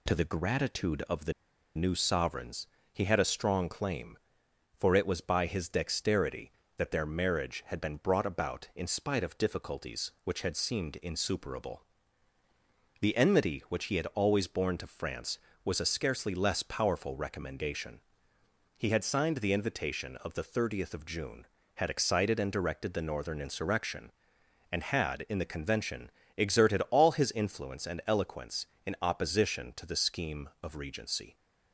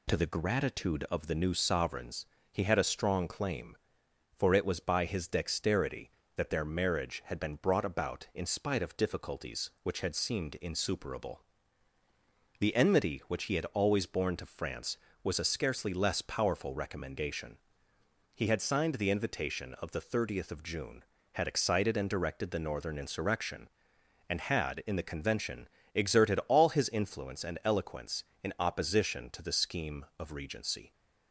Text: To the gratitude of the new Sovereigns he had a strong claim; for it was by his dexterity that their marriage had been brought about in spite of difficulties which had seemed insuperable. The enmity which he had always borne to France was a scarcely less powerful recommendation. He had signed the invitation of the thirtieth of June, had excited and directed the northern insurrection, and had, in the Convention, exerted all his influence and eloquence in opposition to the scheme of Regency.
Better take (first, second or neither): second